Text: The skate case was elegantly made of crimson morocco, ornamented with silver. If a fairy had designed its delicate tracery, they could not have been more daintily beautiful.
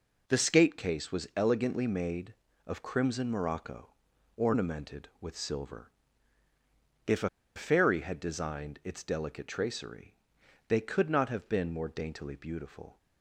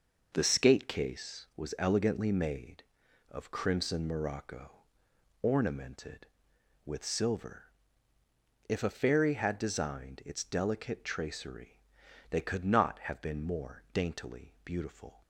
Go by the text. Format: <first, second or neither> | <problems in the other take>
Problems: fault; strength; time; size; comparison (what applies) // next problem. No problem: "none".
second | pauses between "a" and "fairy"; slight; at 7.2 s; 0.27 s long